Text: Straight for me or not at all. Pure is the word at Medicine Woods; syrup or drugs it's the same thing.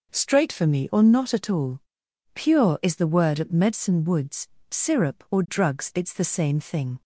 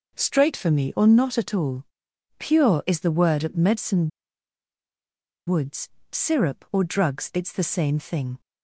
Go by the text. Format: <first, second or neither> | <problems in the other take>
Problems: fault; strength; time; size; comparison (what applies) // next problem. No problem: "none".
first | pauses between "Medicine" and "Woods"; strong; at 4.0 s; 1.3 s long